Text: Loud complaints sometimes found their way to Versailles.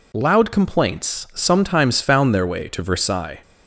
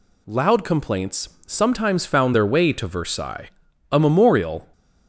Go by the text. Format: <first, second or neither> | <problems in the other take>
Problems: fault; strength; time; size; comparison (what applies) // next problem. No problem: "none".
first | pauses between "complaints" and "sometimes"; slight; at 1.3 s; 0.16 s long // goes on to say "A memorial"; noticeable; from 3.9 s on; 0.76 s long